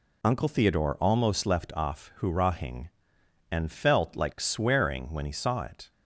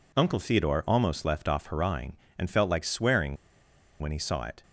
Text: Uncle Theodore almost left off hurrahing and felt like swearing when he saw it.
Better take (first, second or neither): first